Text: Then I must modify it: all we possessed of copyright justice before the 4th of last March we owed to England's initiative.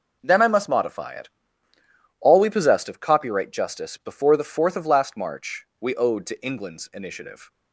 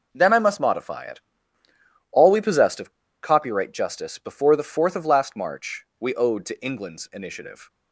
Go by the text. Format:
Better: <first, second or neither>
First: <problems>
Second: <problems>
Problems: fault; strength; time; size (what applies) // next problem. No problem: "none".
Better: first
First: none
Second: pauses between "of" and "copyright"; slight; at 2.9 s; 0.31 s long